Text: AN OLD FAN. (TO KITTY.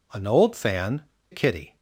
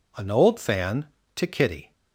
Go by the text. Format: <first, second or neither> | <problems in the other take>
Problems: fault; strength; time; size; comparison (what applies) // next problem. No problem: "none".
second | skips "TO"; at 1.1 s